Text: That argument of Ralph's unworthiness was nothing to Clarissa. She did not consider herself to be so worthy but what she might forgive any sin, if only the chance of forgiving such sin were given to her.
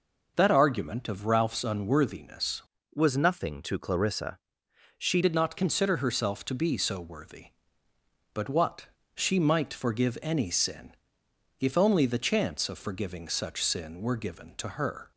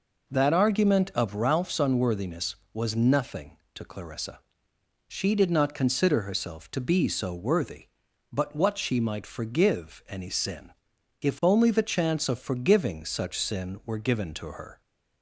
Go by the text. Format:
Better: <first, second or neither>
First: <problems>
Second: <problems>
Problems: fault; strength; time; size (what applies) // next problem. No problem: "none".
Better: second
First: changes voice from "was" to "She"; from 2.9 to 5.2 s; 2.3 s long // pauses between "what" and "she"; slight; at 8.8 s; 0.28 s long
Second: none